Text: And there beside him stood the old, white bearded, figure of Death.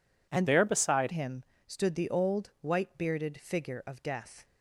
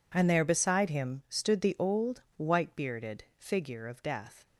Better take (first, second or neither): second